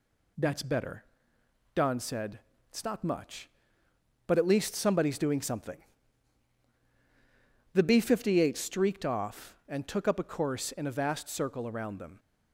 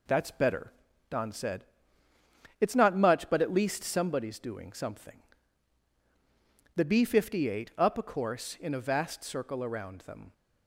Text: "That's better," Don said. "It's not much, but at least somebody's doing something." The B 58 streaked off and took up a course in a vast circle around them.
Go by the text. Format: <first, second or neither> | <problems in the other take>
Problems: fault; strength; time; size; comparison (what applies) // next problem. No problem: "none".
first | skips "streaked off and took"; at 7.7 s